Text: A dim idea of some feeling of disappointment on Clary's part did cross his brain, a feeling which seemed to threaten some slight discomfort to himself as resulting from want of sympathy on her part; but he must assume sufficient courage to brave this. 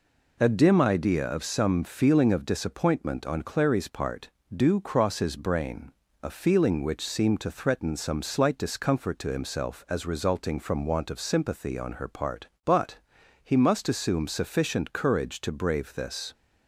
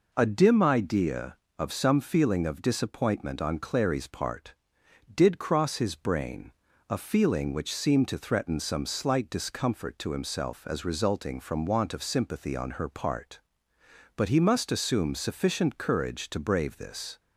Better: second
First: says "do" for "did"; at 4.5 s // pauses between "but" and "he"; noticeable; at 12.9 s; 0.48 s long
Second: none

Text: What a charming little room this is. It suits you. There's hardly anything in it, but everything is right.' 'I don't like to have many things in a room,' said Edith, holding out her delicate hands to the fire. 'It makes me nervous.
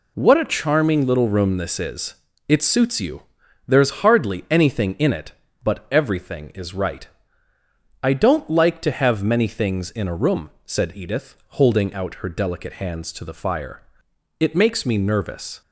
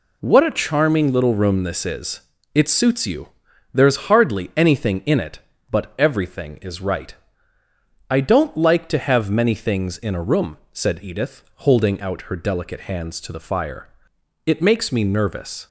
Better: neither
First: none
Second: none

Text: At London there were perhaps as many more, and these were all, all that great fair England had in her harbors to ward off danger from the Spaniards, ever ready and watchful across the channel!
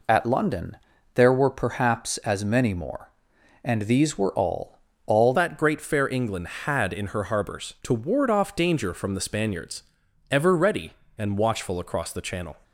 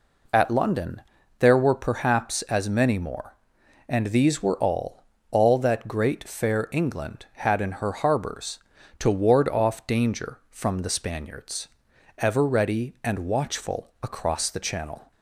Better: second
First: pauses between "London" and "there"; slight; at 0.7 s; 0.36 s long // changes voice at "that"; from 5.3 s on; 7.2 s long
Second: pauses between "London" and "there"; slight; at 1.0 s; 0.36 s long

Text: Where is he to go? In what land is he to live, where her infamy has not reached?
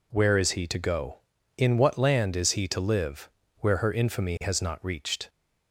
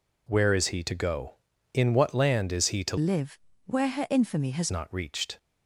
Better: first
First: none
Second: changes voice from "live" to "has"; from 2.9 to 4.7 s; 1.8 s long

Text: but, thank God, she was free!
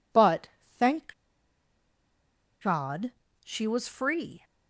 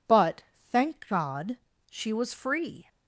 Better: second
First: pauses between "thank" and "God"; strong; at 1.1 s; 1.4 s long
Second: none

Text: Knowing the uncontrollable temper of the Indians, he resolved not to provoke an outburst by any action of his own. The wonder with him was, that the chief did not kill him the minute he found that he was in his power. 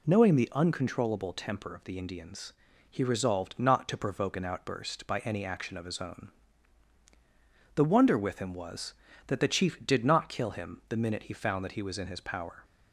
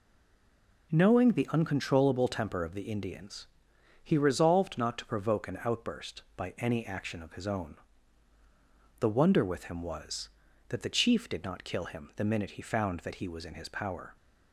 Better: first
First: none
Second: stays silent before the first word; slight; until 0.9 s; 0.9 s long

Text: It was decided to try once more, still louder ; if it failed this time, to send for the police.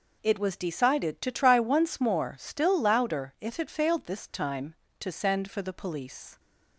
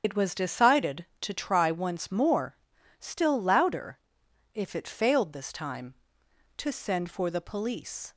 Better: first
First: none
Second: loses the start of "It"; at 0.0 s; 85 ms // starts louder than the rest; strong; until 1.0 s; 7.5 dB

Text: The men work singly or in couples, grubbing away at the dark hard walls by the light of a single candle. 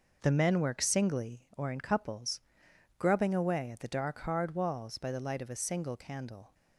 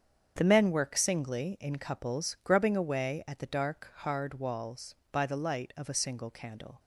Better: first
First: none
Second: starts louder than the rest; strong; until 1.3 s; 7.5 dB // skips "or"; at 1.5 s

